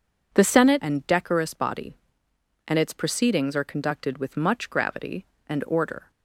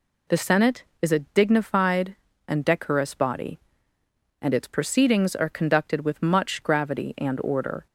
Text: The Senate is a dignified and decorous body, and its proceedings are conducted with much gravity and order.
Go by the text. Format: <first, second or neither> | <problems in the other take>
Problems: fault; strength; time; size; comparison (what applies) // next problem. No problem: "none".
second | skips "is a dignified"; at 0.8 s